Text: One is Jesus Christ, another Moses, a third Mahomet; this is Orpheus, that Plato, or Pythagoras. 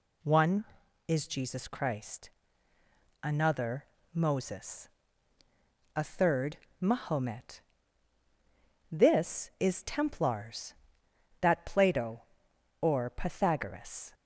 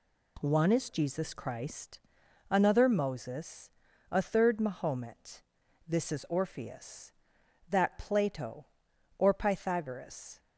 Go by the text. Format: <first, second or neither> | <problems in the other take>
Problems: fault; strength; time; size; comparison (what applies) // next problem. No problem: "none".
second | pauses between "another" and "Moses"; slight; at 3.8 s; 0.28 s long // pauses between "third" and "Mahomet"; slight; at 6.5 s; 0.20 s long // says "Templars" for "Orpheus"; at 9.8 s